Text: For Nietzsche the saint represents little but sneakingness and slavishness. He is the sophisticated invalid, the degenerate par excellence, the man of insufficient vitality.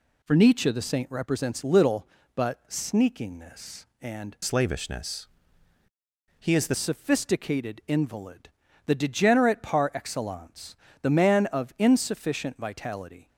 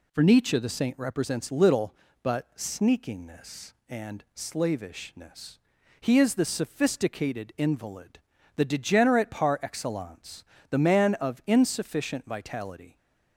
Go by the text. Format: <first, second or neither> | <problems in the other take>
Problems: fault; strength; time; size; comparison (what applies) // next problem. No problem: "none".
second | changes voice from "slavishness" to "the"; from 4.4 to 6.7 s; 2.3 s long